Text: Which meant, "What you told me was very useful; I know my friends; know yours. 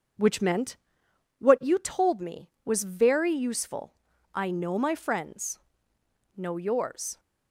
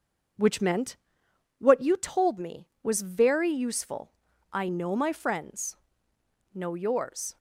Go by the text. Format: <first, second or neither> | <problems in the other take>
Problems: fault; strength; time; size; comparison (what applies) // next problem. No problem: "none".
neither | starts louder than the rest; the same in both